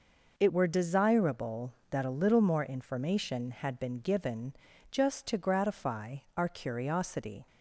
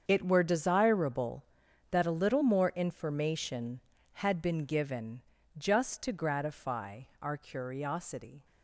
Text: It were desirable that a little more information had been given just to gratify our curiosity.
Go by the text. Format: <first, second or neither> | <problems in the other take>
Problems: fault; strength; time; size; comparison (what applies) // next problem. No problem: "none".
first | gets quieter; strong; throughout; 13 dB // pauses between "given" and "just"; slight; at 5.2 s; 0.34 s long; also in the first // pauses between "gratify" and "our"; slight; at 7.0 s; 0.20 s long; slight in the first